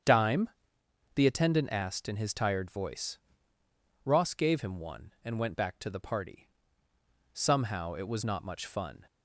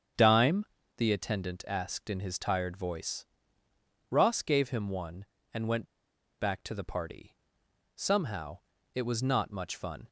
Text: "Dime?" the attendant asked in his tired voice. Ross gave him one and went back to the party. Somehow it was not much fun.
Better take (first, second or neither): first